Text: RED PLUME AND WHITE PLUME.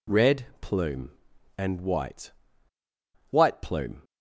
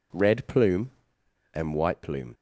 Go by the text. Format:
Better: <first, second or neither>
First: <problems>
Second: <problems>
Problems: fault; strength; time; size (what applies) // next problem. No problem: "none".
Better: second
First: pauses between "RED" and "PLUME"; slight; at 0.4 s; 0.16 s long // says "WHITE" twice; at 3.2 s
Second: none